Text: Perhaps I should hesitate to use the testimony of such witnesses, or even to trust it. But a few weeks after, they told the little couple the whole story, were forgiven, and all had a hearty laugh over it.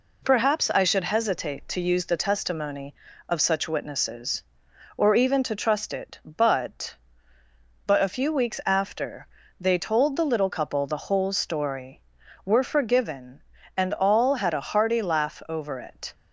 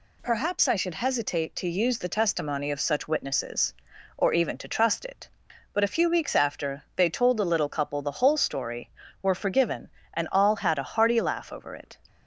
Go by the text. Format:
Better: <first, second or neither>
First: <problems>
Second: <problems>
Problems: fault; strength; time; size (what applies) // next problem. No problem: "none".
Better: second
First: says "But" twice; at 7.8 s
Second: none